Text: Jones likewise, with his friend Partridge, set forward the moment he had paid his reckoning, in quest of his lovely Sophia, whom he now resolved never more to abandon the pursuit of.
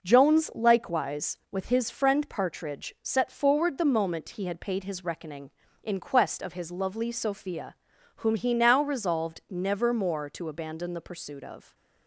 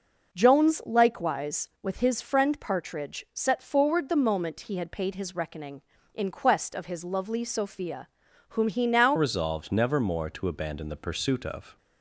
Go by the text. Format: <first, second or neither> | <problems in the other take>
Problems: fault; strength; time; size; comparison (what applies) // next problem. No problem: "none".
first | changes voice at "resolved"; from 9.1 s on; 2.6 s long